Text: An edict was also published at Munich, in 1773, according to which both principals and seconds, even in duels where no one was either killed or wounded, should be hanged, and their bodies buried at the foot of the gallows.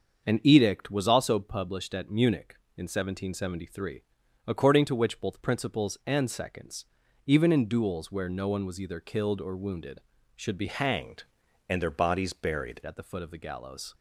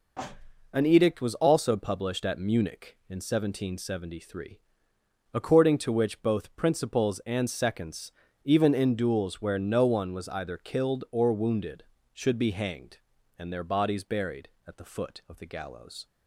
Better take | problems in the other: second | starts louder than the rest; until 1.2 s; 6.5 dB // changes voice from "hanged" to "buried"; from 10.6 to 12.8 s; 2.2 s long

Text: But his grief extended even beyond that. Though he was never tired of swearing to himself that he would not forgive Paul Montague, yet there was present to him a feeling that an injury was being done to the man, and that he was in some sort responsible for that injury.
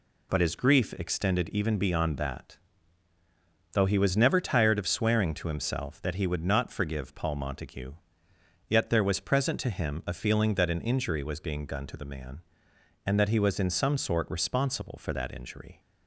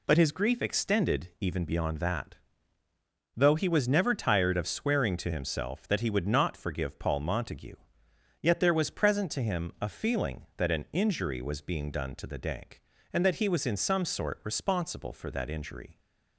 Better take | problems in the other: first | says "dank" for "man"; at 12.3 s

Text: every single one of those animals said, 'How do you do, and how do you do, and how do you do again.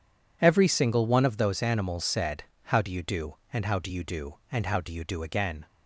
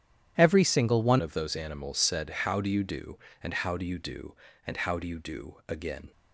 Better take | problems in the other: first | starts louder than the rest; strong; until 1.3 s; 10.5 dB // changes voice at "of"; from 1.2 s on; 4.9 s long

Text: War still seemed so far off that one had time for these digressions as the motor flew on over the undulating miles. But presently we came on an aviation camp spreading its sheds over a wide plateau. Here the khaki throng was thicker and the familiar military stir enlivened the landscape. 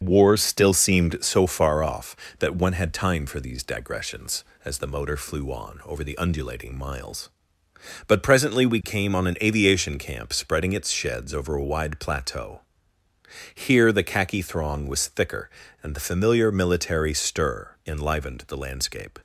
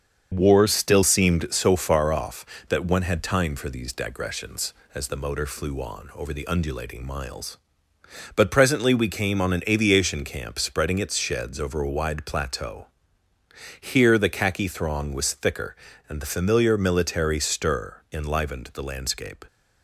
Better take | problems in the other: neither | starts louder than the rest; the same in both

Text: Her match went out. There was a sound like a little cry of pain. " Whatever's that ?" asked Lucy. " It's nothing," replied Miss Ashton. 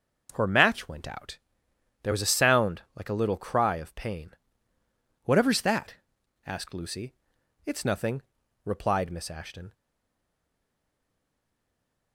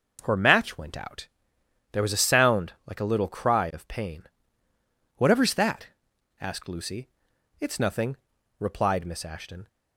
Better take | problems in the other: second | starts louder than the rest; until 1.3 s; 6.5 dB; also in the second // stays silent after the last word; from 9.7 s on; 2.4 s long

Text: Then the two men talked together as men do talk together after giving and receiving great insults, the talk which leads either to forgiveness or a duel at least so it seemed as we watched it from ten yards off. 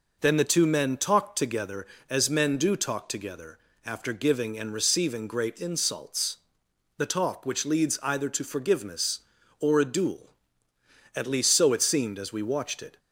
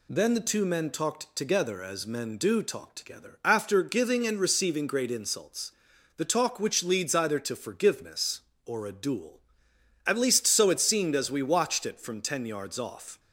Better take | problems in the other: second | pauses between "together" and "after"; slight; at 3.5 s; 0.28 s long // stops before "from ten yards off"; at 12.9 s

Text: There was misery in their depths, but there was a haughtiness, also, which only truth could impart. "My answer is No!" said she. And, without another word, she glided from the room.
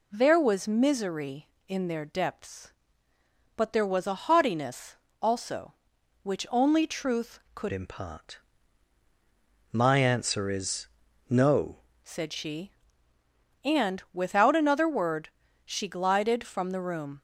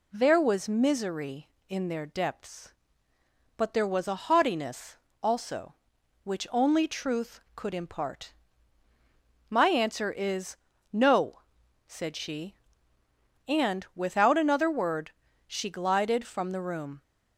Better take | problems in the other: second | changes voice from "impart" to "No"; from 7.7 to 11.7 s; 4.0 s long // pauses between "is" and "No"; at 10.8 s; 0.42 s long; slight in the second

